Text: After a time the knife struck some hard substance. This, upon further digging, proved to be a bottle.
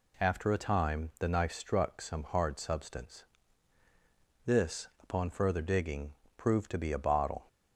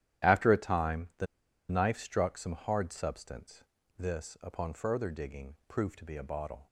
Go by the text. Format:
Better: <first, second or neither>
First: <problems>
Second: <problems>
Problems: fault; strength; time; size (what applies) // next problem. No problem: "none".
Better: first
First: none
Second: starts louder than the rest; strong; until 1.7 s; 11.5 dB // pauses between "the" and "knife"; at 1.2 s; 0.44 s long